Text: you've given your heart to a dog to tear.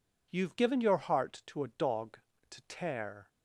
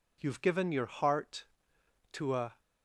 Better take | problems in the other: first | stops before "dog to tear"; at 2.5 s

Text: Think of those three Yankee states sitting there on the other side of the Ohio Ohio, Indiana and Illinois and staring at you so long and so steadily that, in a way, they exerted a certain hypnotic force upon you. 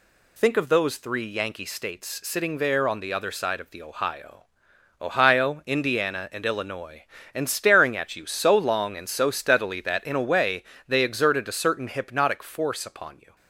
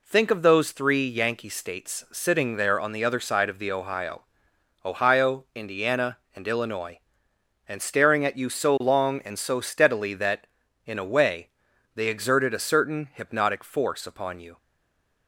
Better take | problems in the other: first | pauses between "Ohio" and "Ohio"; noticeable; at 4.2 s; 0.62 s long; noticeable in the first // stays silent after the last word; slight; from 14.5 s on; 0.7 s long

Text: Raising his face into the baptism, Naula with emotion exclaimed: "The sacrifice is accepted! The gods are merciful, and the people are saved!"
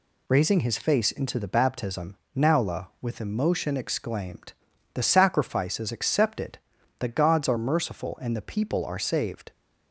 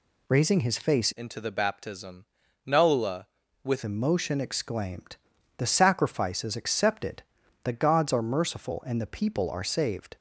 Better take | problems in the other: first | changes voice from "into" to "with"; from 1.1 to 3.8 s; 2.7 s long

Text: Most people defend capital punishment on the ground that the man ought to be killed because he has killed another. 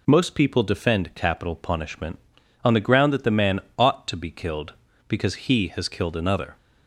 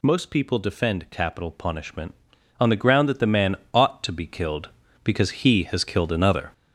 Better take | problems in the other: first | gets louder; throughout; 6.5 dB // pauses between "man" and "ought"; slight; at 3.5 s; 0.20 s long; slight in the first

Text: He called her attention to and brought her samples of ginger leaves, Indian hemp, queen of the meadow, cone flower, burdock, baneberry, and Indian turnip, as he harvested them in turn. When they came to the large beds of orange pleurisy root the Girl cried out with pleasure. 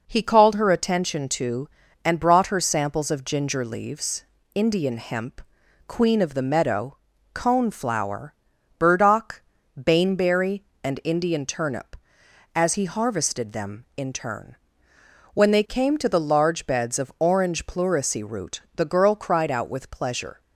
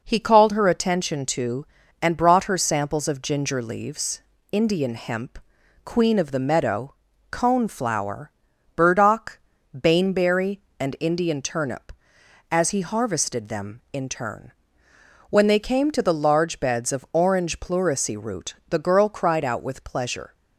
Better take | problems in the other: neither | none

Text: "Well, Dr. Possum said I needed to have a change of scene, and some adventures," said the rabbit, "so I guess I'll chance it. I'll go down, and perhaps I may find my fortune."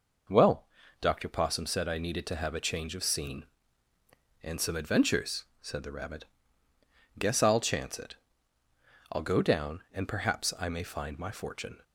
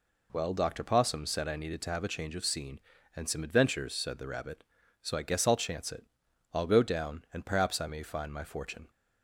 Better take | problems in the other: second | skips "so I"; at 6.7 s

